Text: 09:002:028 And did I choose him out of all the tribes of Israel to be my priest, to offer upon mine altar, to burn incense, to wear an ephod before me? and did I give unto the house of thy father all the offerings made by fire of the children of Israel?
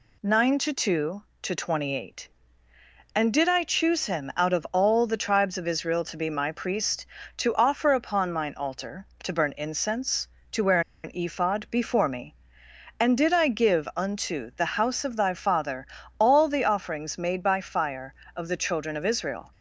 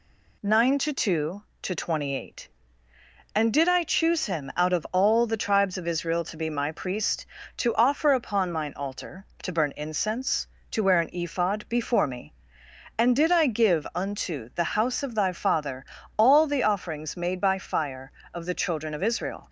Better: second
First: pauses between "wear" and "an"; slight; at 10.8 s; 0.23 s long // pauses between "father" and "all"; slight; at 15.8 s; 0.32 s long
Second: pauses between "father" and "all"; slight; at 15.8 s; 0.32 s long

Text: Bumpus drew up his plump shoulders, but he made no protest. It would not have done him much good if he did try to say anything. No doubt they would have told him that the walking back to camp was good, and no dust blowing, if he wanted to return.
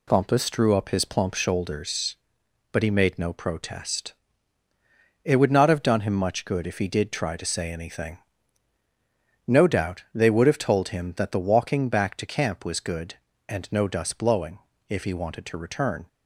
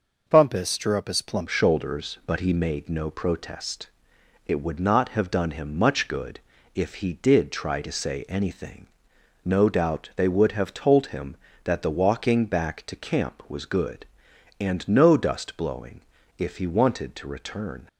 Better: first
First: none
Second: changes voice at "shoulders"; from 1.4 s on; 16.4 s long // pauses between "good" and "if"; slight; at 6.4 s; 0.34 s long

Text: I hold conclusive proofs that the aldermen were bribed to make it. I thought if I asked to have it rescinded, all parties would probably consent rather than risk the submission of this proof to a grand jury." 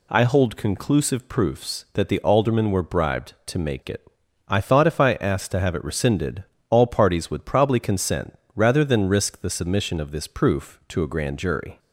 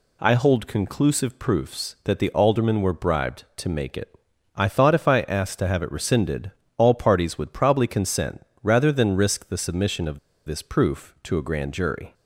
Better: first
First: pauses between "consent" and "rather"; slight; at 8.3 s; 0.20 s long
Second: pauses between "consent" and "rather"; slight; at 8.4 s; 0.20 s long // pauses between "of" and "this"; slight; at 10.1 s; 0.28 s long

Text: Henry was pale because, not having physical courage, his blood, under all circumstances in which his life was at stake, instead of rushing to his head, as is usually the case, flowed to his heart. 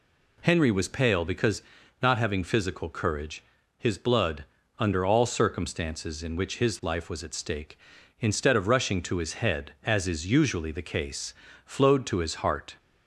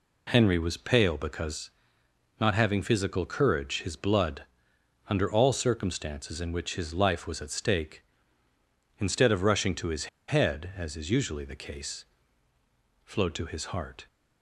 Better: first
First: none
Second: pauses between "his" and "head"; slight; at 10.0 s; 0.21 s long

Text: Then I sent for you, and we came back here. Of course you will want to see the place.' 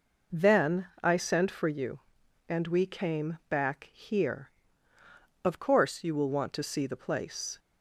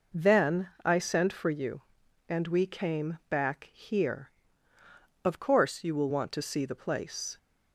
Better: neither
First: pauses between "Then" and "I"; slight; at 0.8 s; 0.16 s long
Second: pauses between "Then" and "I"; slight; at 0.6 s; 0.16 s long

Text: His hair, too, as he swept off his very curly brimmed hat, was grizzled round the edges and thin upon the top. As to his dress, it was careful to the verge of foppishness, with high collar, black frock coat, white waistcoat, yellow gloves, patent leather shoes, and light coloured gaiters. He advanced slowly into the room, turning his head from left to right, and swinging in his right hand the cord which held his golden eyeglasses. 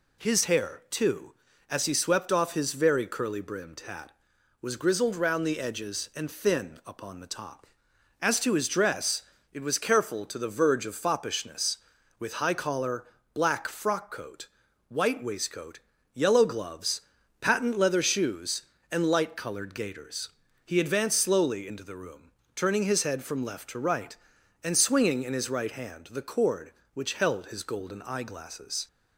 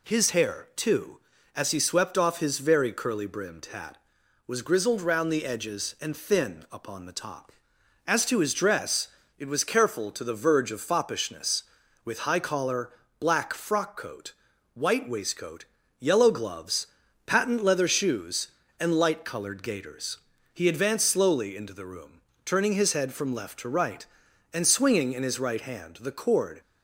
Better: first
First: none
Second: stops before "which held his golden eyeglasses"; at 26.6 s

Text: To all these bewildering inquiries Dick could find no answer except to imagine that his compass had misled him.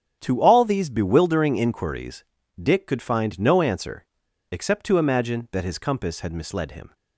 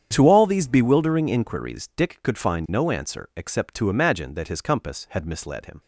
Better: second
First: starts louder than the rest; strong; until 1.2 s; 9 dB // pauses between "inquiries" and "Dick"; at 2.2 s; 0.38 s long // pauses between "answer" and "except"; noticeable; at 4.0 s; 0.46 s long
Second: starts louder than the rest; strong; until 1.1 s; 8.5 dB

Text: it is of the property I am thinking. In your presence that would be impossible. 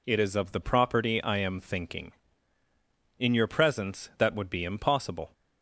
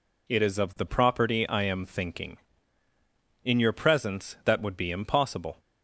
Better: neither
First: none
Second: none

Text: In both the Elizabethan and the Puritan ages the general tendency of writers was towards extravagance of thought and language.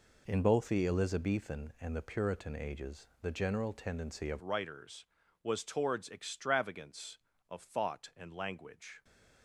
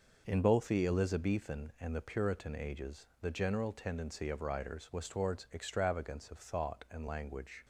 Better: second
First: changes voice at "writers"; from 4.4 s on; 4.6 s long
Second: none

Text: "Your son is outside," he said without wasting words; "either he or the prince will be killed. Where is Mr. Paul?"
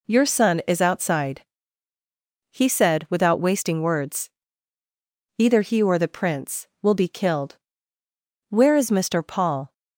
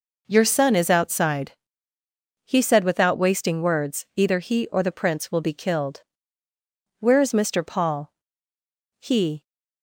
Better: first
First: none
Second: goes on to say "He"; slight; from 9.0 s on; 0.42 s long

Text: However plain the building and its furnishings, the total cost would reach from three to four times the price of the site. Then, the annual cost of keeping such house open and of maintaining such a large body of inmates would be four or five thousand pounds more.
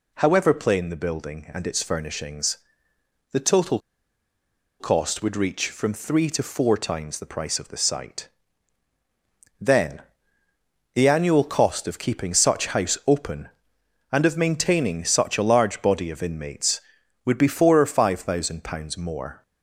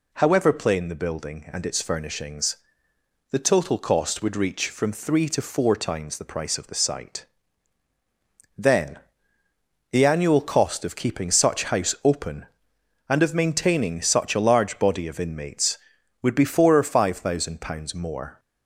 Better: second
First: pauses between "total" and "cost"; at 3.7 s; 1.0 s long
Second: none

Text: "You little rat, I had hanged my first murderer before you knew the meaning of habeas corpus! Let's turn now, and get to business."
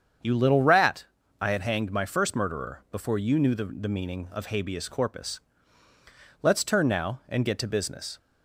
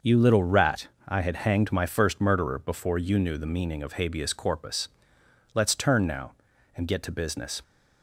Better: second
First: starts louder than the rest; strong; until 1.5 s; 7.5 dB // says "the" twice; at 3.6 s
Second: starts louder than the rest; noticeable; until 1.2 s; 6 dB

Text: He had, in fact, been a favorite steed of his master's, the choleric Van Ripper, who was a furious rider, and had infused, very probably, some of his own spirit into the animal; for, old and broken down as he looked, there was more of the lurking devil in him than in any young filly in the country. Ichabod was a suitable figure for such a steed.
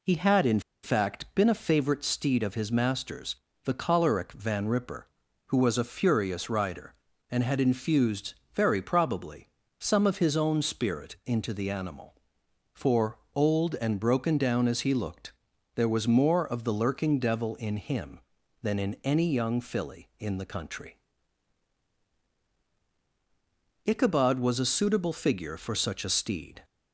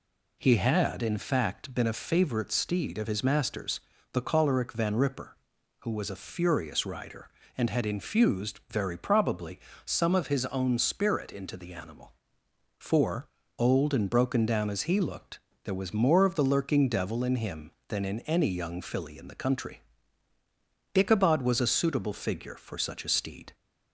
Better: second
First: pauses between "in" and "fact"; slight; at 0.5 s; 0.23 s long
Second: none

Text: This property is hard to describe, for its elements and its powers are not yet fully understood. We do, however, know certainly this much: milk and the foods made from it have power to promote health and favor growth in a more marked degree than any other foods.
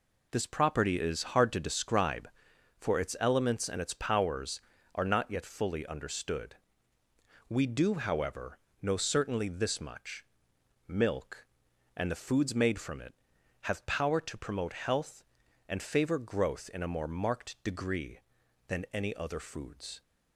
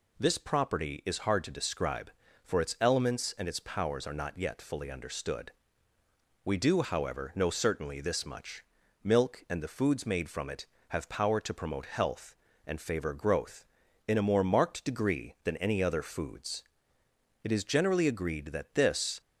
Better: first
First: none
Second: goes on to say "It is generally agreed that this"; strong; from 17.4 s on; 1.7 s long

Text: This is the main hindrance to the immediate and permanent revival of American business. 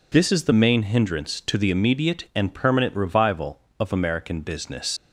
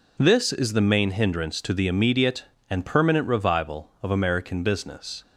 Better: second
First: leaves "business" unfinished; at 4.9 s; 100 ms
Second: none

